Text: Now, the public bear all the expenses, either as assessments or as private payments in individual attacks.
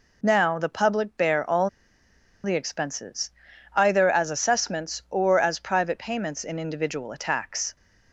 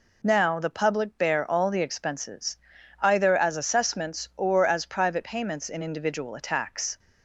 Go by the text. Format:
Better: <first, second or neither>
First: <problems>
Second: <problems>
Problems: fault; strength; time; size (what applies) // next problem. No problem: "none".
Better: second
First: pauses between "all" and "the"; noticeable; at 1.6 s; 0.76 s long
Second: none